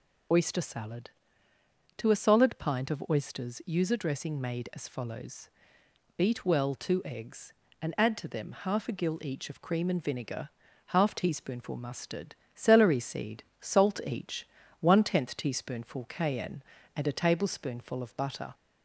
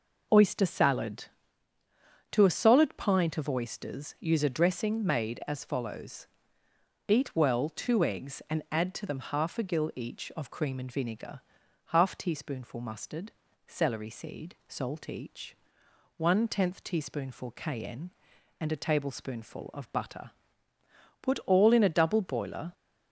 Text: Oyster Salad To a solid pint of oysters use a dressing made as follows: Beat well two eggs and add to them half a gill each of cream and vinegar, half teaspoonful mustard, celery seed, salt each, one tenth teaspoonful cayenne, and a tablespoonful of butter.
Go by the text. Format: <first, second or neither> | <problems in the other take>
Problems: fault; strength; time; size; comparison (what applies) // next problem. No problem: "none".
first | goes on to say "Put all in a double boiler"; from 21.2 s on; 1.5 s long